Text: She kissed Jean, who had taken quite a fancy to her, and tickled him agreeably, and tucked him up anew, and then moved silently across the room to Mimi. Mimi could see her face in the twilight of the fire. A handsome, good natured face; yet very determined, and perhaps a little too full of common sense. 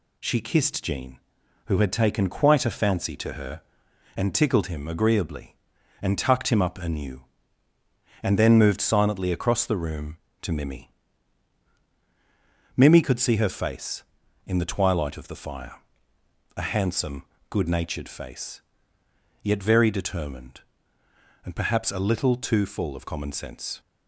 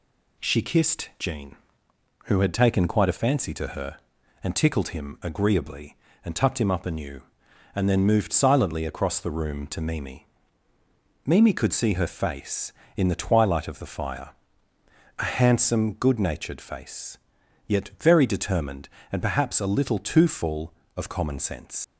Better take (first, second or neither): first